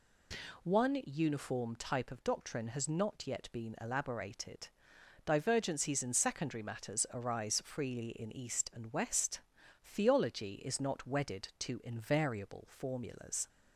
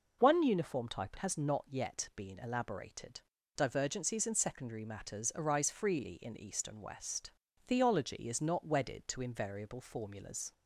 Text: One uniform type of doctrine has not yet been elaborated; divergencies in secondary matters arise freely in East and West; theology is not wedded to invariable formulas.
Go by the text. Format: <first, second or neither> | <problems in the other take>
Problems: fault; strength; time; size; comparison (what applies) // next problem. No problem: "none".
first | skips "of doctrine"; at 1.1 s